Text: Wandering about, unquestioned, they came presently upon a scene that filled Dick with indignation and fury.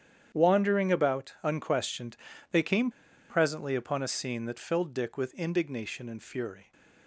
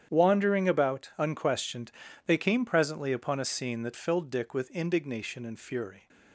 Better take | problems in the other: second | starts louder than the rest; strong; until 1.4 s; 9 dB; strong in the second // pauses between "came" and "presently"; at 2.9 s; 0.39 s long

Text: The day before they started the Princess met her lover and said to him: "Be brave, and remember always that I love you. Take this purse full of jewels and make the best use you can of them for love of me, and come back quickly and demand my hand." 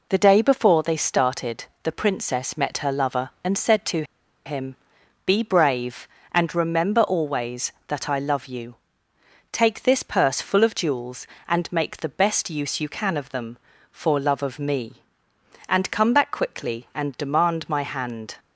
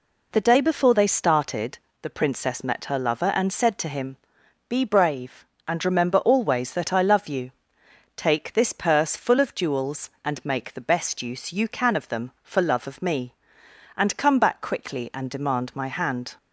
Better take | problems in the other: second | pauses between "started" and "the"; slight; at 1.6 s; 0.18 s long; slight in the second // pauses between "to" and "him"; at 4.0 s; 0.41 s long

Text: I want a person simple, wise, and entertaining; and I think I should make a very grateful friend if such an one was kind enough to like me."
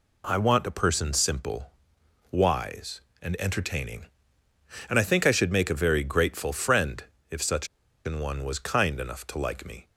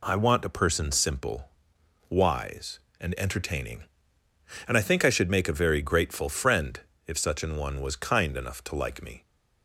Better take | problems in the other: second | pauses between "friend" and "if"; slight; at 7.0 s; 0.26 s long; slight in the second // pauses between "such" and "an"; at 7.6 s; 0.38 s long

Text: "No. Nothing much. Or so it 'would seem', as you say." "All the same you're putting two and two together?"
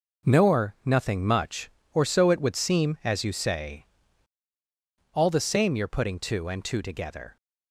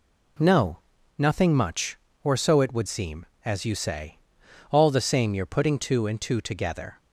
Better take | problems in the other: second | says "Nor" for "No"; at 0.2 s

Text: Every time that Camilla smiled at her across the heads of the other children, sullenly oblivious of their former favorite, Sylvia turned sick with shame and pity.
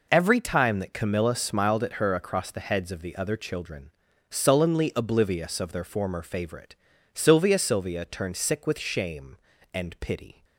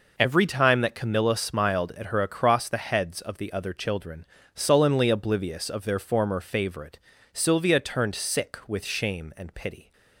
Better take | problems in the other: second | says "Sylvia" twice; at 7.5 s

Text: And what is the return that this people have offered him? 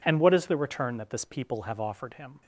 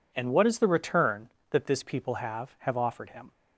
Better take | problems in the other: first | says "have" twice; at 2.6 s

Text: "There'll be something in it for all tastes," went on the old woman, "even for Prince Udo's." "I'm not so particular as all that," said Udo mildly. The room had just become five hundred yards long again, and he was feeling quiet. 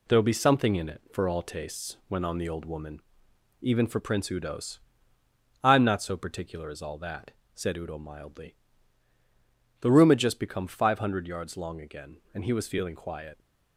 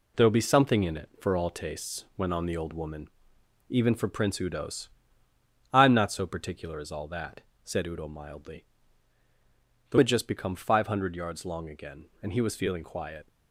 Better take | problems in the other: first | skips "room"; at 9.9 s

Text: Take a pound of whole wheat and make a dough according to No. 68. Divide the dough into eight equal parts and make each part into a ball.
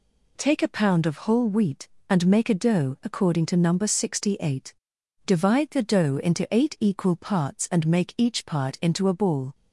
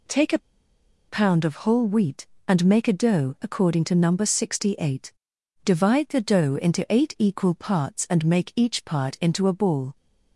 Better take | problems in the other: first | pauses between "a" and "pound"; noticeable; at 0.3 s; 0.69 s long

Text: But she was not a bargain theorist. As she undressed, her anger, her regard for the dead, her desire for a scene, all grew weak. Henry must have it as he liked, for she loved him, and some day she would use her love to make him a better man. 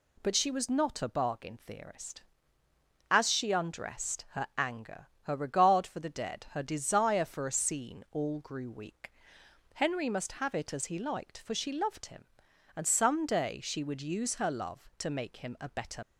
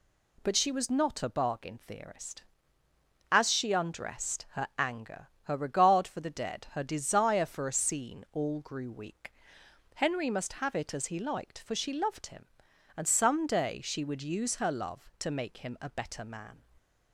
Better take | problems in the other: second | stops before "man"; at 16.0 s

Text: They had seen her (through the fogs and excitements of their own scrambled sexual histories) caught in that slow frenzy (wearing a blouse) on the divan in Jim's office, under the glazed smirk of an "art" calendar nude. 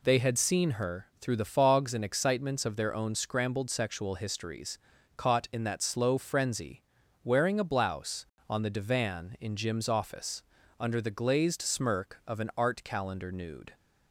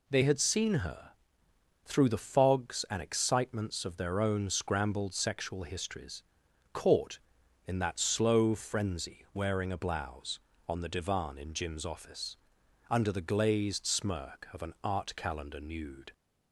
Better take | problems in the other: first | changes voice at "had"; from 0.2 s on; 15.9 s long

